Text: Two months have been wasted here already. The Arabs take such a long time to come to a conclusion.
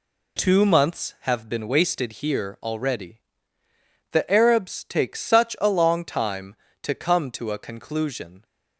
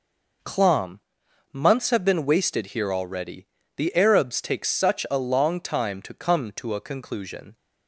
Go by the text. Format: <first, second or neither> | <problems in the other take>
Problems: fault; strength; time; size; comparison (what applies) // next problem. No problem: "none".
first | says "Clom" for "Two"; at 0.4 s